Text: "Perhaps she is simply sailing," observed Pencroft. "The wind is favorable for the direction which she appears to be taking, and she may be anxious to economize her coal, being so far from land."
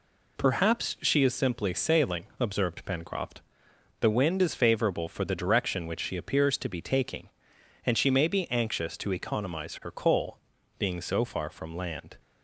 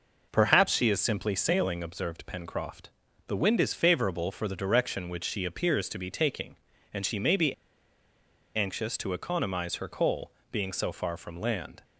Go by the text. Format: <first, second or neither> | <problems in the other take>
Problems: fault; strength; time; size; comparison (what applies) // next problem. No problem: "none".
first | pauses between "be" and "anxious"; at 7.5 s; 1.0 s long